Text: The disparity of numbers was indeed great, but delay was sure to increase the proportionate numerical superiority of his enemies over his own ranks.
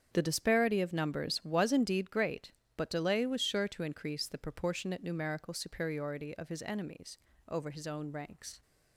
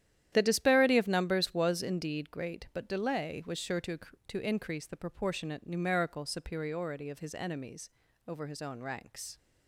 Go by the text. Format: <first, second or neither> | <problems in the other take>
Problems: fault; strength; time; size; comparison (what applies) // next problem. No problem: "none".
first | starts louder than the rest; strong; until 1.3 s; 11 dB; strong in the first // says "to" twice; at 4.2 s // pauses between "enemies" and "over"; slight; at 7.9 s; 0.34 s long; slight in the first